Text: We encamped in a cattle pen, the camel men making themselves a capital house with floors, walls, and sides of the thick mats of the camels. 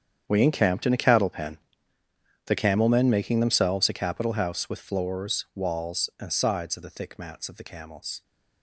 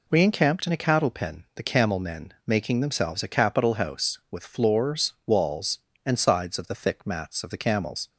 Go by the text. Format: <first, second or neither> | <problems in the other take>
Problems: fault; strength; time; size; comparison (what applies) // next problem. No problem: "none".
second | gets quieter; strong; throughout; 15 dB